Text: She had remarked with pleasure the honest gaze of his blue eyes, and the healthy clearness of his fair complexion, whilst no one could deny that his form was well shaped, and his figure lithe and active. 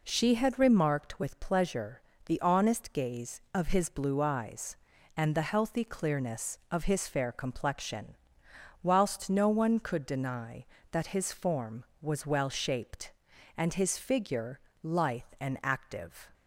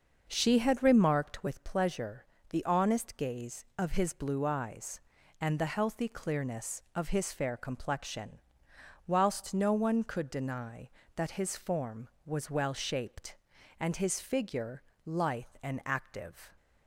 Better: first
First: pauses between "pleasure" and "the"; slight; at 2.0 s; 0.24 s long // pauses between "figure" and "lithe"; slight; at 14.5 s; 0.22 s long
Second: starts louder than the rest; noticeable; until 1.6 s; 6 dB // pauses between "pleasure" and "the"; slight; at 2.2 s; 0.24 s long // pauses between "figure" and "lithe"; slight; at 14.8 s; 0.22 s long

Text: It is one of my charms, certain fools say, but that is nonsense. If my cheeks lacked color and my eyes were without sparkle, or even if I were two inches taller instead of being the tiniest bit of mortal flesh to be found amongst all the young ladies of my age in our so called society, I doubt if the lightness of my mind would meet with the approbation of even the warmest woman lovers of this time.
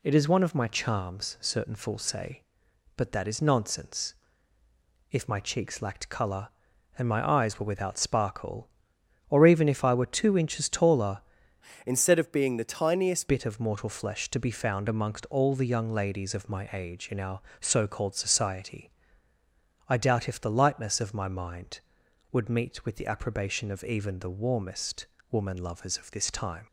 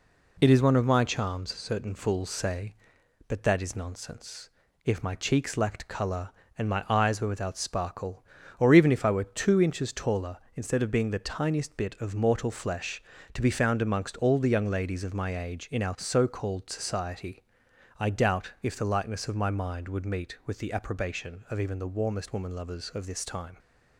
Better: second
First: changes voice from "instead" to "tiniest"; from 11.8 to 13.2 s; 1.4 s long // pauses between "warmest" and "woman"; slight; at 25.0 s; 0.24 s long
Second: none

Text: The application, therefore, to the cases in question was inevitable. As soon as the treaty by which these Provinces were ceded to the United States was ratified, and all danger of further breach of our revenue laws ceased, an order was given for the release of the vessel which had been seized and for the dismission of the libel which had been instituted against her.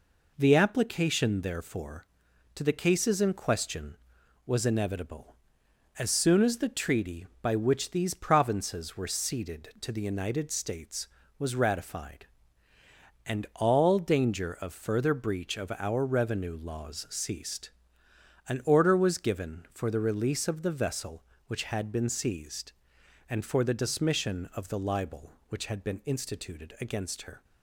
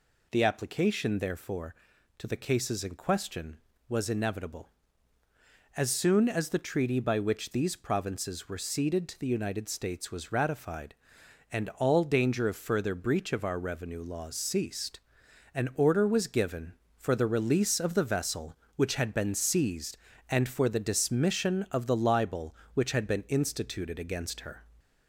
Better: first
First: none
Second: gets louder; slight; throughout; 2.5 dB

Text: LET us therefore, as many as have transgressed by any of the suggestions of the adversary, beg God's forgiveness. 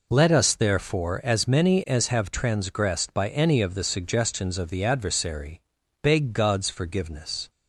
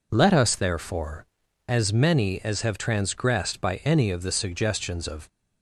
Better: first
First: none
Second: stops before "the adversary beg God's forgiveness"; at 5.2 s

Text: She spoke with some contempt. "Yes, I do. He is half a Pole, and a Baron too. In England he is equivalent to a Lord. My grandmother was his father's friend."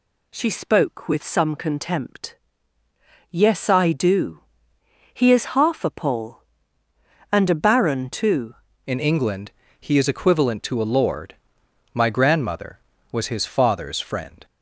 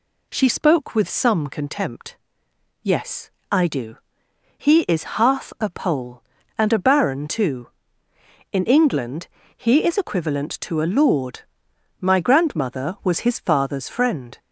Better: second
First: changes voice at "In"; from 8.8 s on; 5.6 s long // pauses between "England" and "he"; slight; at 9.5 s; 0.30 s long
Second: pauses between "England" and "he"; slight; at 9.2 s; 0.30 s long

